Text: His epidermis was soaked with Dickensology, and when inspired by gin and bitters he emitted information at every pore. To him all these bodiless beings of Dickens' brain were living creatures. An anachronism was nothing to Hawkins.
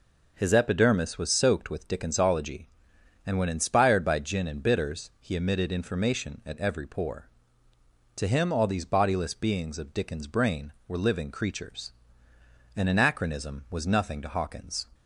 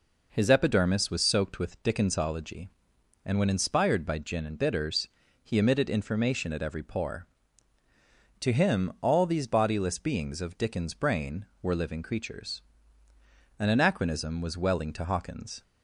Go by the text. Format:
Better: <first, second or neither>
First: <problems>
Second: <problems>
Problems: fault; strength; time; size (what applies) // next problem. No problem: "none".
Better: first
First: none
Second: pauses between "bitters" and "he"; slight; at 5.0 s; 0.34 s long // says "welling" for "nothing"; at 14.5 s